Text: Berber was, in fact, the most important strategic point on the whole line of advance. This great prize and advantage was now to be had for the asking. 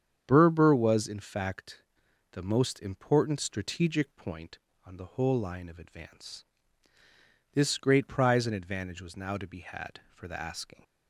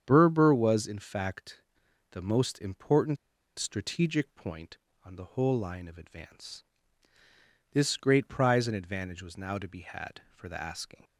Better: first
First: starts louder than the rest; strong; until 1.2 s; 8 dB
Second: starts louder than the rest; strong; until 1.0 s; 8 dB // pauses between "important" and "strategic"; at 3.1 s; 0.42 s long

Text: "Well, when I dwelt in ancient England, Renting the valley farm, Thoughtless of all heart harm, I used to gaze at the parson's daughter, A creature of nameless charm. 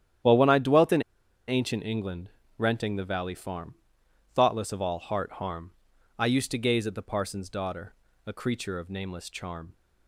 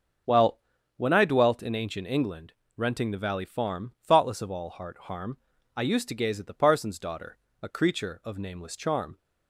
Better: second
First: starts louder than the rest; strong; until 1.7 s; 10.5 dB // pauses between "in" and "ancient"; noticeable; at 1.0 s; 0.46 s long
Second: starts louder than the rest; noticeable; until 1.6 s; 6 dB

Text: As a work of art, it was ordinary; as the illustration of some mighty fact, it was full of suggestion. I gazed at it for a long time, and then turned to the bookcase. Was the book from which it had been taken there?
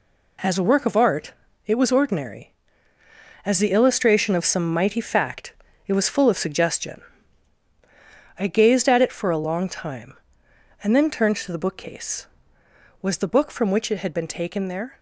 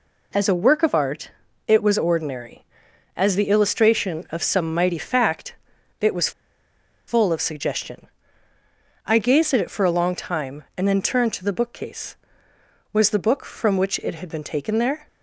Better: first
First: none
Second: pauses between "was" and "full"; noticeable; at 6.3 s; 0.77 s long

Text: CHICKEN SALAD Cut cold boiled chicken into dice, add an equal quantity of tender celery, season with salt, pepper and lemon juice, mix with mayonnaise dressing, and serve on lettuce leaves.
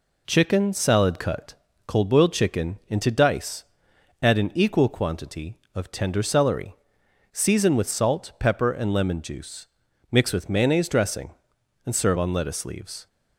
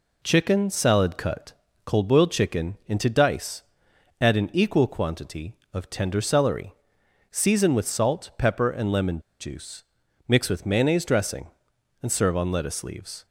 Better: first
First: pauses between "Cut" and "cold"; slight; at 1.5 s; 0.32 s long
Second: pauses between "Cut" and "cold"; slight; at 1.5 s; 0.32 s long // pauses between "lemon" and "juice"; slight; at 9.1 s; 0.21 s long

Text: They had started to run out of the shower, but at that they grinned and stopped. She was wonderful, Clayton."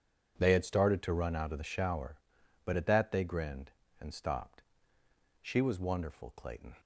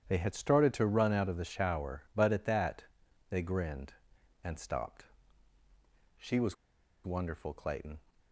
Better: first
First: none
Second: starts louder than the rest; strong; until 1.1 s; 9.5 dB // pauses between "that" and "they"; noticeable; at 2.8 s; 0.46 s long // pauses between "was" and "wonderful"; noticeable; at 6.5 s; 0.50 s long

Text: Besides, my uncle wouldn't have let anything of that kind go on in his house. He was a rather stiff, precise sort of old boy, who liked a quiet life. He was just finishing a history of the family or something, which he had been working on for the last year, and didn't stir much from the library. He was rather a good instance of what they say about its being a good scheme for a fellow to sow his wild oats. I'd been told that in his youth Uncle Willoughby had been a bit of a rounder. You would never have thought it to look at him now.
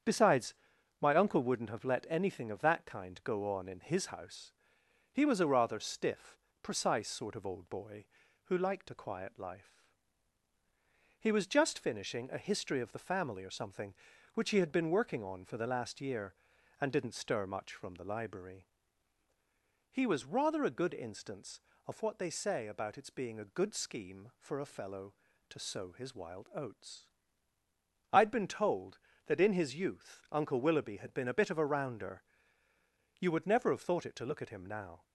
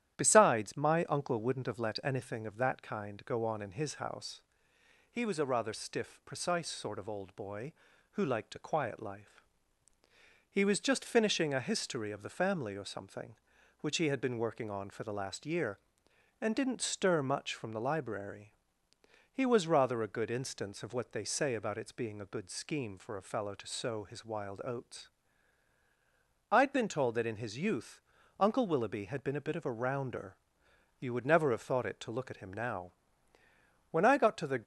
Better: first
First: starts louder than the rest; strong; until 1.5 s; 8 dB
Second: starts louder than the rest; strong; until 1.1 s; 11.5 dB // pauses between "youth" and "Uncle"; at 27.9 s; 0.40 s long // goes on to say "When I got to the"; noticeable; from 33.8 s on; 0.74 s long

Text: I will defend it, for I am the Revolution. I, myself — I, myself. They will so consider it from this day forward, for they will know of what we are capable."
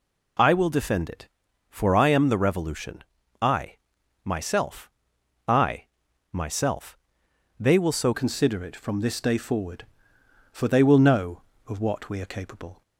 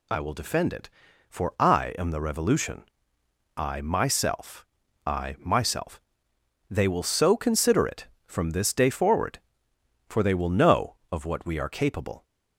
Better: second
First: changes voice at "consider"; from 8.1 s on; 4.7 s long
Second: none

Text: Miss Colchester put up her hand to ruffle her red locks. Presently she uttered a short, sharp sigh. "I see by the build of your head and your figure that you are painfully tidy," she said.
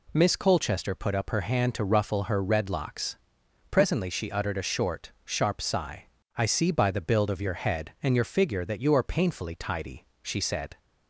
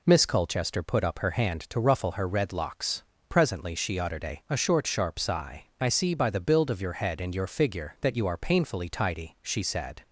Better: first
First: none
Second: says "a" twice; at 4.4 s

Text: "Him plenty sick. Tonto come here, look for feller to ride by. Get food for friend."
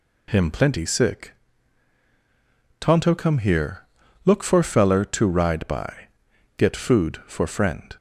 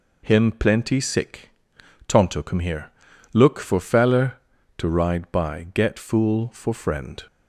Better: first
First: none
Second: says "fool" for "food"; at 5.9 s

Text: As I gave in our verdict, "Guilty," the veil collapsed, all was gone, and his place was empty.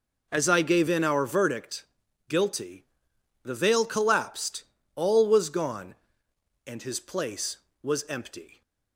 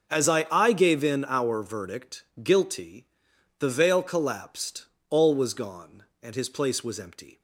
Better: first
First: none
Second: starts louder than the rest; until 1.1 s; 6.5 dB // says "I" twice; at 0.5 s

